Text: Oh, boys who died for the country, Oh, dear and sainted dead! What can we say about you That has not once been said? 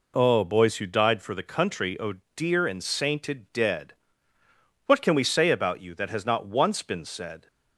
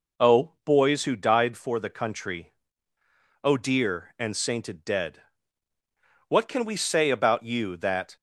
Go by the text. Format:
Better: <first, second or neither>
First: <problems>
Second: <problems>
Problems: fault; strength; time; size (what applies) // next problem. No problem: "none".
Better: first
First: none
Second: stops before "has not once been said"; at 8.1 s